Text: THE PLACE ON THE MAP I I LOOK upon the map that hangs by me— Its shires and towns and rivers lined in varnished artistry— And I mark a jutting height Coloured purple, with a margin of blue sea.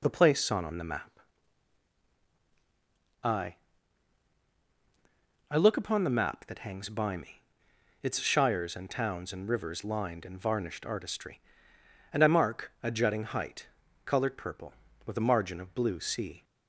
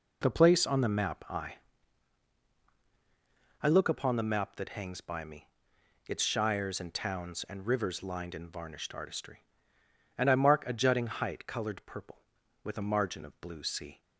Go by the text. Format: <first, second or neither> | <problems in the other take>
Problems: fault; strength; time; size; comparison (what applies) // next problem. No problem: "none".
second | says "ON" twice; at 0.6 s // pauses between "MAP" and "I"; strong; at 1.1 s; 2.0 s long // pauses between "I" and "I"; strong; at 3.5 s; 1.9 s long; strong in the second // pauses between "height" and "Coloured"; slight; at 13.6 s; 0.36 s long